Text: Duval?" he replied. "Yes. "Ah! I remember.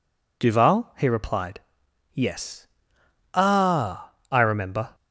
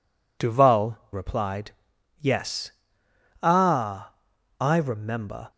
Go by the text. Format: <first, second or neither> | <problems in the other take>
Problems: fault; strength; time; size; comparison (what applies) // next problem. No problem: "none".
first | skips "he"; at 1.0 s